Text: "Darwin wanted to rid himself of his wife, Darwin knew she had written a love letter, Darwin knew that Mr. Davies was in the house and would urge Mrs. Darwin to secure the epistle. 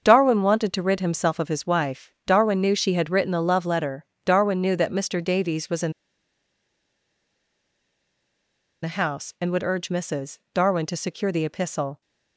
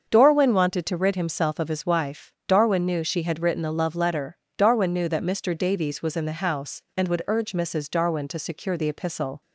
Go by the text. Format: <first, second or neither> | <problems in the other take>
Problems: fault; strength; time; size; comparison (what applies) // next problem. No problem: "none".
second | starts louder than the rest; until 1.0 s; 7 dB; also in the second // pauses between "in" and "the"; strong; at 5.9 s; 2.9 s long